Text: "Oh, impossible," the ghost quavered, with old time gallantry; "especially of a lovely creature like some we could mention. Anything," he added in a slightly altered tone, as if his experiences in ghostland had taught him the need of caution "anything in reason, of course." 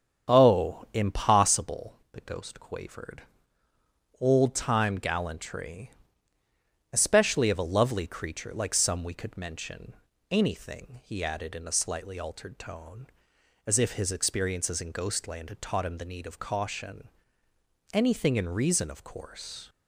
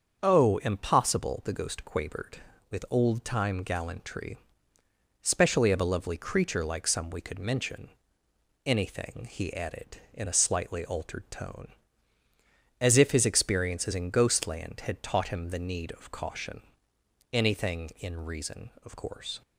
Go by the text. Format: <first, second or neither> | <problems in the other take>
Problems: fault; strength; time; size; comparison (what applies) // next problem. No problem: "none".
second | starts louder than the rest; strong; until 1.3 s; 7.5 dB; also in the second // skips "with"; at 3.7 s // pauses between "caution" and "anything"; noticeable; at 17.0 s; 0.86 s long; noticeable in the second